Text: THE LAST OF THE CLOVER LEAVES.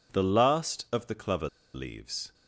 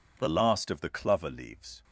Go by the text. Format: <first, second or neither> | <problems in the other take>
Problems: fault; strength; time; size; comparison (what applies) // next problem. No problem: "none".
second | pauses between "CLOVER" and "LEAVES"; slight; at 1.4 s; 0.25 s long